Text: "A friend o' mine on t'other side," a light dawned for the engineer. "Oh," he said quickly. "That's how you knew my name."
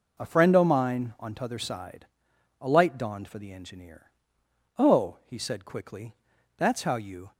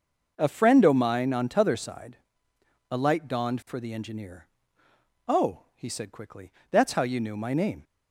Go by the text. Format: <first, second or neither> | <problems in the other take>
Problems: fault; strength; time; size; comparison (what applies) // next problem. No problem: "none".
second | stops before "knew my name"; at 7.3 s